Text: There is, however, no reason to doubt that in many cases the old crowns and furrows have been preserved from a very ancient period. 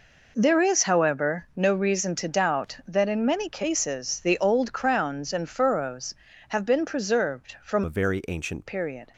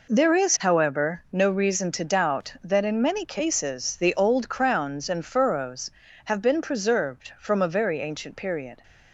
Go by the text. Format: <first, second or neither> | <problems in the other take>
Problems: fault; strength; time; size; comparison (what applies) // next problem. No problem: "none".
second | changes voice from "a" to "ancient"; from 7.8 to 8.6 s; 0.8 s long